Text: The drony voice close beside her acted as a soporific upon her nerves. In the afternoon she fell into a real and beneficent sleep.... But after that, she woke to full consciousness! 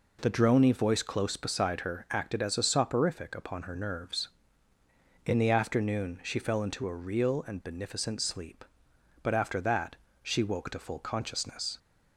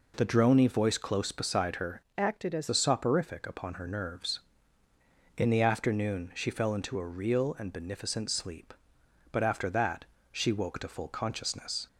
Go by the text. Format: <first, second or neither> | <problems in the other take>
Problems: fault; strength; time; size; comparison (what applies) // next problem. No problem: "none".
first | changes voice from "acted" to "as"; from 2.1 to 2.6 s; 0.5 s long